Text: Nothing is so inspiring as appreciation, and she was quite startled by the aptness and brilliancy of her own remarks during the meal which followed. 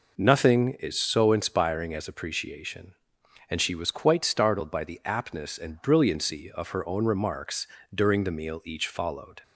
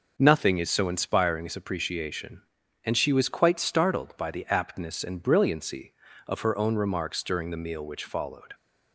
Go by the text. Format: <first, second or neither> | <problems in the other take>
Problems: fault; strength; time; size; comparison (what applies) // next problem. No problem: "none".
second | pauses between "remarks" and "during"; slight; at 7.6 s; 0.30 s long // says "each" for "which"; at 8.6 s